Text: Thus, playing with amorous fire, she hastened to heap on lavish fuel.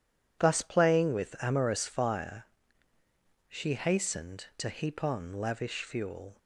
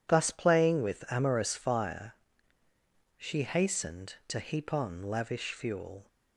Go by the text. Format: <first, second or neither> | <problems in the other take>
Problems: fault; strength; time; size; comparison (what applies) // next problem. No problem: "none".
neither | none